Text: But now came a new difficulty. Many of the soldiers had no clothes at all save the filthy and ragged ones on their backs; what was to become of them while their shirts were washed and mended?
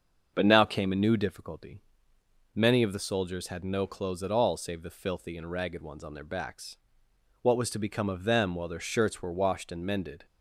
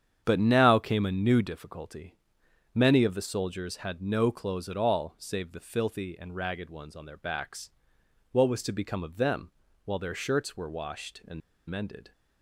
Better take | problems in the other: first | starts louder than the rest; strong; until 1.2 s; 8.5 dB; also in the first // pauses between "them" and "while"; slight; at 9.5 s; 0.34 s long // pauses between "and" and "mended"; slight; at 11.4 s; 0.29 s long

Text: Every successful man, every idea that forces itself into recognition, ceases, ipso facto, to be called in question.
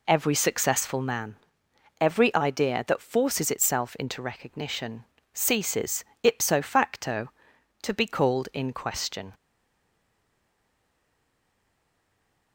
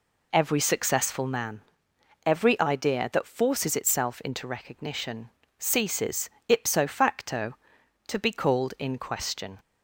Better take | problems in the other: second | stays silent after the last word; strong; from 9.3 s on; 3.2 s long

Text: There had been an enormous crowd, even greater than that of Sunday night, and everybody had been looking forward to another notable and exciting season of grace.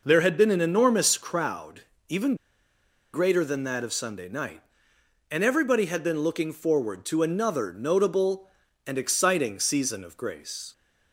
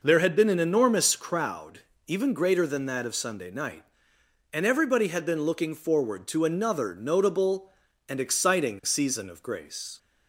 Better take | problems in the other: second | pauses between "even" and "greater"; noticeable; at 2.3 s; 0.79 s long

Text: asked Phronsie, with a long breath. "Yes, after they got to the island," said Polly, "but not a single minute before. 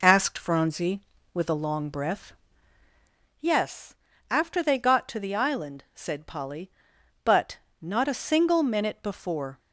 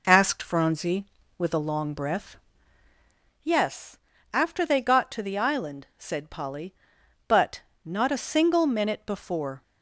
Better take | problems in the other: neither | pauses between "but" and "not"; slight; the same in both

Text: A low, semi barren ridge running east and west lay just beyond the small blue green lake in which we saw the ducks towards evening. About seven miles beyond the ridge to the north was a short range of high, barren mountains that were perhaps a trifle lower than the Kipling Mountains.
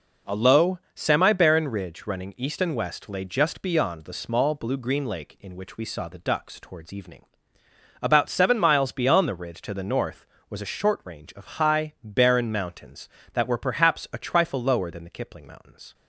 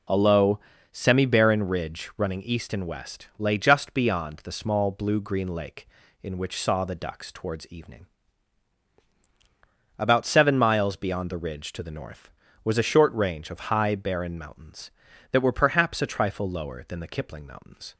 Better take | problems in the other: first | skips "we"; at 6.6 s

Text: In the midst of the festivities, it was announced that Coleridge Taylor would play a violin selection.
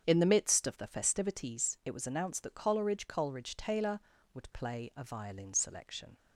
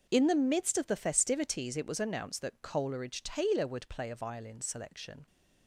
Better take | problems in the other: second | starts louder than the rest; strong; until 1.0 s; 7.5 dB; also in the second // says "Coleridge" twice; at 3.0 s

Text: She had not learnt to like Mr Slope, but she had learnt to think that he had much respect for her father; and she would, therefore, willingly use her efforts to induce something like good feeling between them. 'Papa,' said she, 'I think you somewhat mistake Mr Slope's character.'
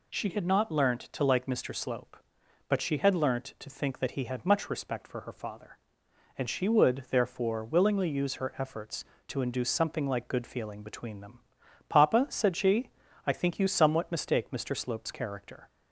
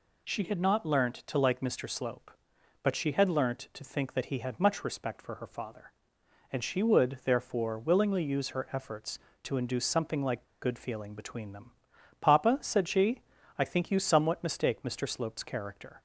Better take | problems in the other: first | pauses between "like" and "good"; slight; at 10.4 s; 0.19 s long

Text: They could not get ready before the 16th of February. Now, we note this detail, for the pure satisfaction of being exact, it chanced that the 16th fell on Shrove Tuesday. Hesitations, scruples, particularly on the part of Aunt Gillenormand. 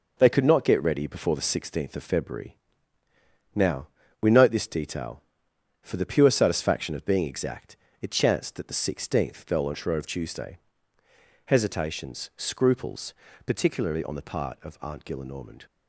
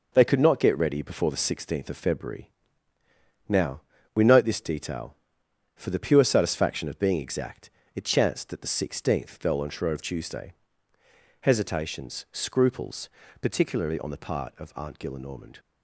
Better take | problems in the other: neither | none

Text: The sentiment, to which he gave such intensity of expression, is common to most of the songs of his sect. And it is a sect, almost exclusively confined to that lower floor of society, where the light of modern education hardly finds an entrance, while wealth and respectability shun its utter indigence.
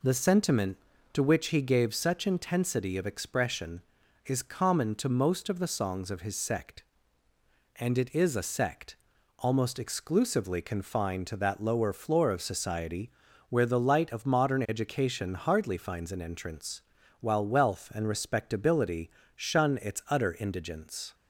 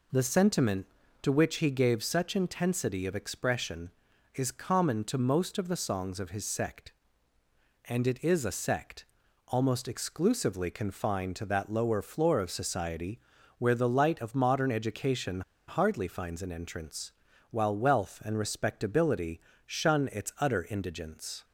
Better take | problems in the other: first | pauses between "education" and "hardly"; slight; at 15.4 s; 0.26 s long // pauses between "respectability" and "shun"; slight; at 19.3 s; 0.28 s long; slight in the first

